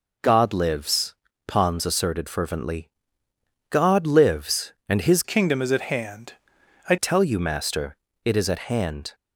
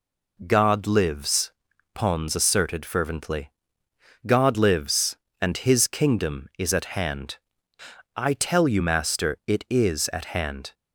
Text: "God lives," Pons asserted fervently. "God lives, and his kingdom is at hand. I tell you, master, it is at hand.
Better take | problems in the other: second | changes voice from "kingdom" to "I"; from 5.2 to 6.9 s; 1.7 s long

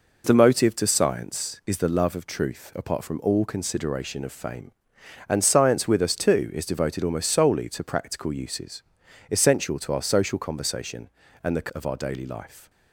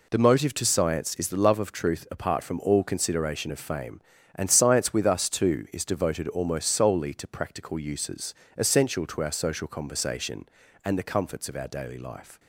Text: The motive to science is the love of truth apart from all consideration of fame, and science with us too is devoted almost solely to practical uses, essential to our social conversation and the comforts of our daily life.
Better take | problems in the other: second | skips "comforts"; at 11.6 s

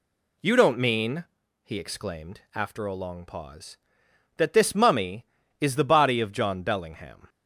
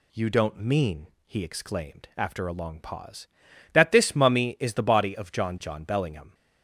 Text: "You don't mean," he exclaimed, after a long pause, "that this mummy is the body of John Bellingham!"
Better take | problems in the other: first | says "John" twice; at 5.6 s

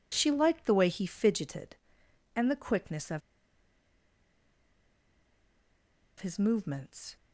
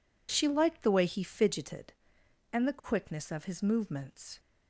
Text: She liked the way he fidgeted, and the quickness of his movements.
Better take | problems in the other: second | pauses between "of" and "his"; strong; at 3.2 s; 2.9 s long

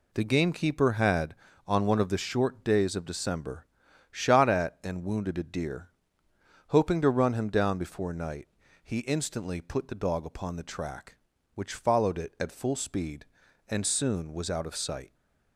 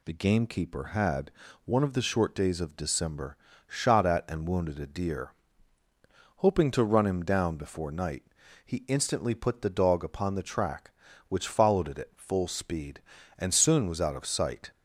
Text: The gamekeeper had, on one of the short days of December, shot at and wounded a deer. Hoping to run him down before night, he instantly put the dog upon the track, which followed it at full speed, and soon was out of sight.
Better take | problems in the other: first | skips "on"; at 1.4 s

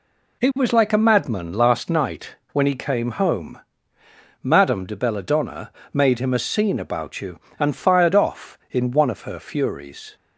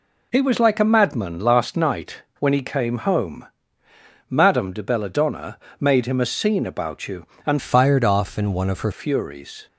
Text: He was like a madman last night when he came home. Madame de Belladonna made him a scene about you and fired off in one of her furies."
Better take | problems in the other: first | pauses between "night" and "when"; slight; at 2.2 s; 0.18 s long; slight in the first // pauses between "Belladonna" and "made"; slight; at 5.5 s; 0.24 s long; slight in the first // changes voice from "fired" to "her"; from 7.5 to 8.9 s; 1.4 s long

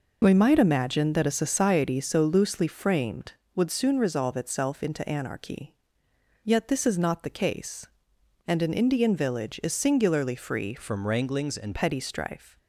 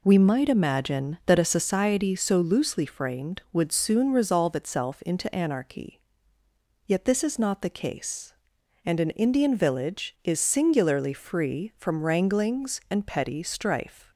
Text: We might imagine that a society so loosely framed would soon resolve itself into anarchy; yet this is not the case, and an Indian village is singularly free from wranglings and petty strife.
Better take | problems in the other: second | changes voice from "from" to "and"; from 10.7 to 11.7 s; 1.0 s long

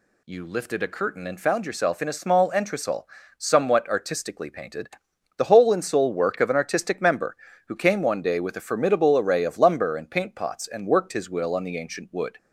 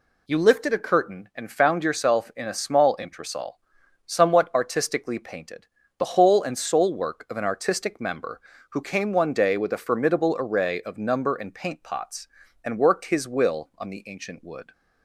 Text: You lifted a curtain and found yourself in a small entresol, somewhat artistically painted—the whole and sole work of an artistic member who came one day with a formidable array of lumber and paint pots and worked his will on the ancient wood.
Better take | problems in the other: first | says "number" for "lumber"; at 10.9 s

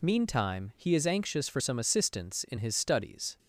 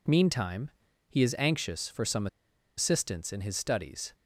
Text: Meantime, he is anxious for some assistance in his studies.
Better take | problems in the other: first | pauses between "some" and "assistance"; noticeable; at 2.2 s; 0.50 s long

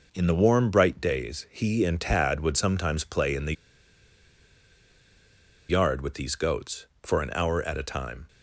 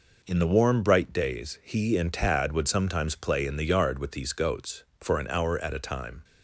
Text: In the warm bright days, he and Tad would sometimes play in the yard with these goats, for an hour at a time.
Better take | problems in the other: second | pauses between "the" and "yard"; strong; at 3.5 s; 2.1 s long

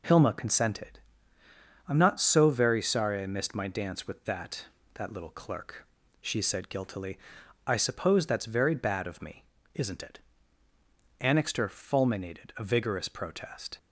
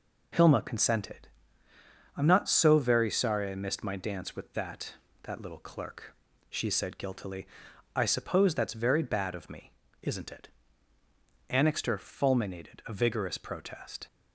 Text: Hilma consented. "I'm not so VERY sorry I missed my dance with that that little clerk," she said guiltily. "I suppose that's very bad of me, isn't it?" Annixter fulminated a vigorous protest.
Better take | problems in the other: neither | none

